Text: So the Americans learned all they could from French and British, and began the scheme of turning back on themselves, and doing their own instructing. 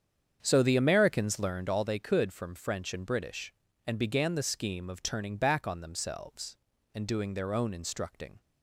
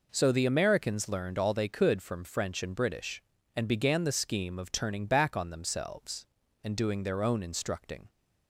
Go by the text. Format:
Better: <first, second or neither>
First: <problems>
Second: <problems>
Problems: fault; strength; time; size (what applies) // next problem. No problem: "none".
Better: second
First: starts louder than the rest; strong; until 1.8 s; 8 dB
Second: none